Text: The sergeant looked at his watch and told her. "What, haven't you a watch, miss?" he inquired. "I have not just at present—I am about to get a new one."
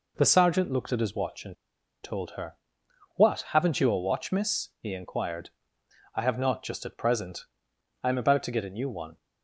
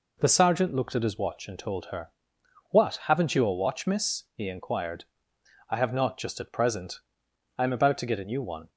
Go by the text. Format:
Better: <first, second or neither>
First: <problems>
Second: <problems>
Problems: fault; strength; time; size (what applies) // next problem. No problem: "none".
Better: second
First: pauses between "and" and "told"; noticeable; at 1.5 s; 0.49 s long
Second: none